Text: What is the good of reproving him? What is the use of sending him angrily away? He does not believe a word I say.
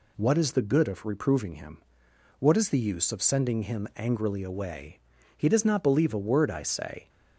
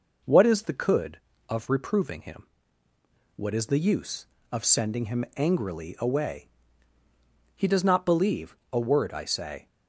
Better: first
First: none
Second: says "could" for "good"; at 0.7 s // pauses between "believe" and "a"; slight; at 8.5 s; 0.16 s long

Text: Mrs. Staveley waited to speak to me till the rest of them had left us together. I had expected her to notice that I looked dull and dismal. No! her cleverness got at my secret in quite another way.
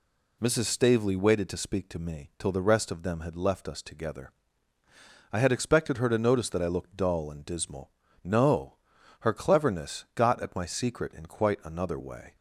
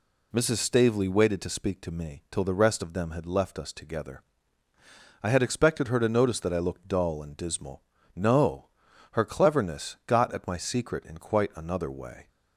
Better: neither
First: none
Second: none

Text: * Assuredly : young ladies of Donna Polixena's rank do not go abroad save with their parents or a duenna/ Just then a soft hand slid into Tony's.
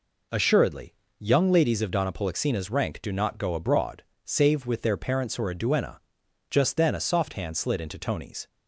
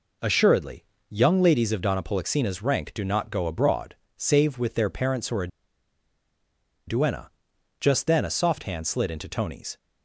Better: first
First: pauses between "abroad" and "save"; slight; at 4.0 s; 0.20 s long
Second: pauses between "abroad" and "save"; slight; at 3.9 s; 0.20 s long // pauses between "a" and "duenna"; strong; at 5.4 s; 1.3 s long

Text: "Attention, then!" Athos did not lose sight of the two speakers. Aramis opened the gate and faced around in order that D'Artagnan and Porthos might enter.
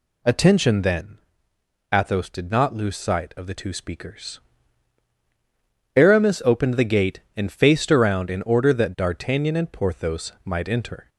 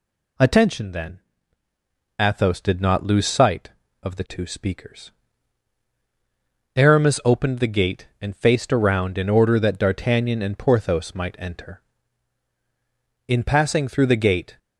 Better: first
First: none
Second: goes on to say "In passing through the gate"; from 13.2 s on; 1.3 s long

